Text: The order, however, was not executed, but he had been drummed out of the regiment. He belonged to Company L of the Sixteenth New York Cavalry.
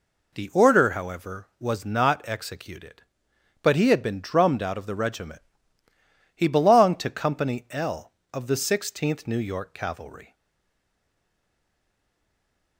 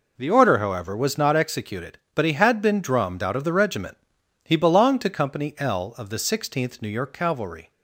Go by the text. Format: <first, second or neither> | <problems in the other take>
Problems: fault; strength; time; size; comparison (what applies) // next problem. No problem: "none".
second | stays silent after the last word; strong; from 10.3 s on; 2.4 s long